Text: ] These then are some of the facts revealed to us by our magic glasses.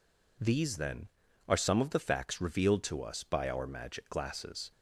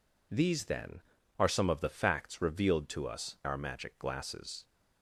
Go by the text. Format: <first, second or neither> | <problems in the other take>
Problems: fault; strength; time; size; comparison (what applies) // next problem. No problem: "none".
first | skips "by"; at 3.4 s